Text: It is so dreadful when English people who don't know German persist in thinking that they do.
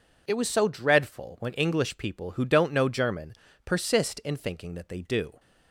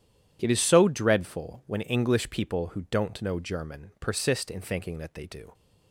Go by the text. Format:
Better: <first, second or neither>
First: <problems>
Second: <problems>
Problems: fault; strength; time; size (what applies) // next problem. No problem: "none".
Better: second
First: says "was" for "is"; at 0.3 s // pauses between "German" and "persist"; slight; at 3.3 s; 0.30 s long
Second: none